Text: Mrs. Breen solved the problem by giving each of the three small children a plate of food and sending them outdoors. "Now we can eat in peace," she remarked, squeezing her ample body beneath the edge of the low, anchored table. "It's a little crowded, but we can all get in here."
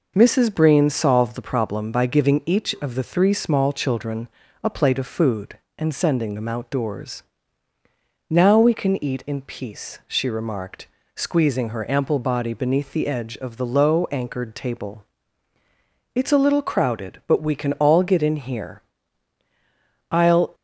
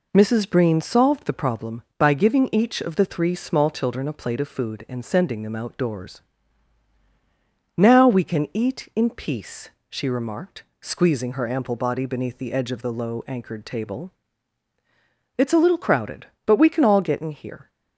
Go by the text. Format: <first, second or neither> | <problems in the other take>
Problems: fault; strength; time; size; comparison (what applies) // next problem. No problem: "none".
second | pauses between "children" and "a"; slight; at 4.2 s; 0.34 s long // goes on to say "I'll"; slight; from 20.1 s on; 0.42 s long